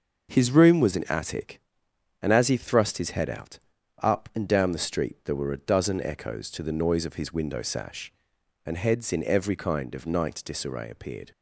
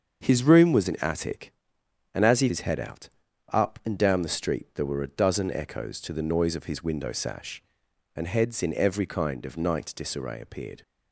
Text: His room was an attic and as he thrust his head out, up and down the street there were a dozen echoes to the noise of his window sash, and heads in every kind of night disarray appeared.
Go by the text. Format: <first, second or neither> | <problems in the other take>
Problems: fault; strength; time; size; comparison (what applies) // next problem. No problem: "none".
first | starts louder than the rest; until 1.2 s; 7 dB; noticeable in the first // skips "thrust"; at 2.4 s